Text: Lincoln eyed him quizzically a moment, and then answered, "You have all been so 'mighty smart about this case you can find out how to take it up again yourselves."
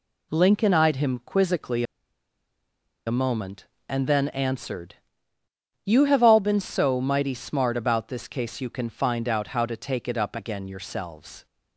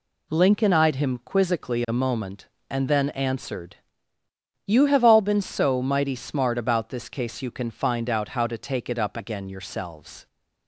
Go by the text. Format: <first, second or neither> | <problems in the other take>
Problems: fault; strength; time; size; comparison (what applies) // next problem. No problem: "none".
second | pauses between "quizzically" and "a"; at 1.8 s; 1.2 s long